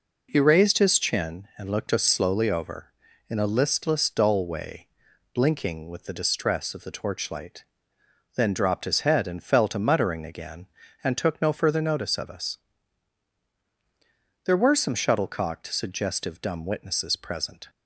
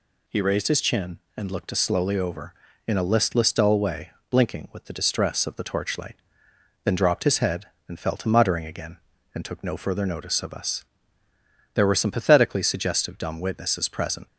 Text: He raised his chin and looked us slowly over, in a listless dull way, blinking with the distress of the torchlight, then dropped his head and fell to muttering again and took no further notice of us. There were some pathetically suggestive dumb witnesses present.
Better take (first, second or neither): second